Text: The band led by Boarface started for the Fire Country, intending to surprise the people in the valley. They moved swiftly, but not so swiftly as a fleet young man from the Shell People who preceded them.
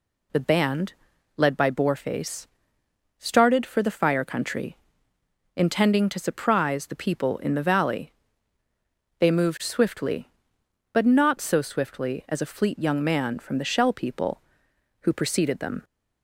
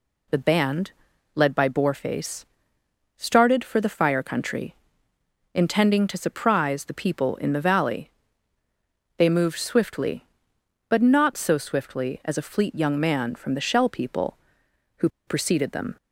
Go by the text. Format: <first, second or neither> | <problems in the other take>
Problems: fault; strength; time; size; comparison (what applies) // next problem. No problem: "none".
first | pauses between "band" and "led"; at 0.9 s; 0.42 s long; also in the first // pauses between "Boarface" and "started"; noticeable; at 2.4 s; 0.72 s long; noticeable in the first // pauses between "who" and "preceded"; slight; at 15.0 s; 0.18 s long